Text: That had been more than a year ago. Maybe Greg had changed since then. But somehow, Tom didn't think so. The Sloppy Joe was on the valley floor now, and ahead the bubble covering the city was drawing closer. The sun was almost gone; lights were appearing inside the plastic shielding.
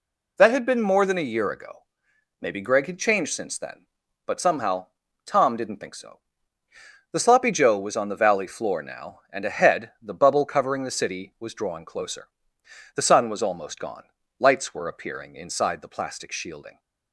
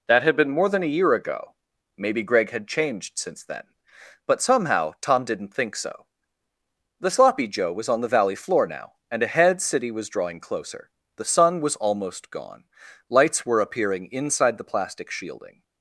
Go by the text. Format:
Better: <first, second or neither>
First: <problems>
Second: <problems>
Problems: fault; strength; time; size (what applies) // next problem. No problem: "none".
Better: first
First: none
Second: skips "the bubble covering the"; at 9.6 s